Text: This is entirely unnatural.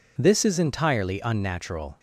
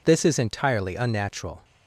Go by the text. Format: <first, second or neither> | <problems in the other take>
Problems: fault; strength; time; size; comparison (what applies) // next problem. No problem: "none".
neither | none